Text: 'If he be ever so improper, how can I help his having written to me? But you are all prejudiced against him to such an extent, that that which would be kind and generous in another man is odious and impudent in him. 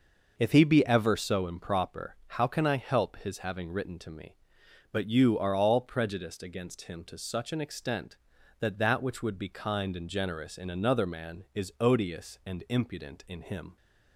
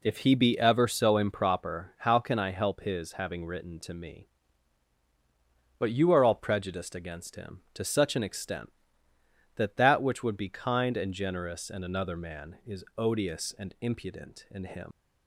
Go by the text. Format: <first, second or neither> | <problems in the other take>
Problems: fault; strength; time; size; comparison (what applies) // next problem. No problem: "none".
first | leaves "him" unfinished; at 14.9 s; 115 ms